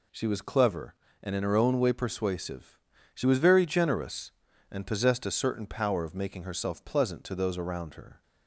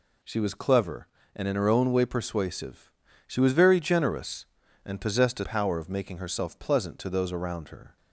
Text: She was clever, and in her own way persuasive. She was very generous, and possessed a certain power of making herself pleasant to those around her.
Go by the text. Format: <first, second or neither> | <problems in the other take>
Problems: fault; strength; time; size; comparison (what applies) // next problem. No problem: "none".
first | skips "certain"; at 5.4 s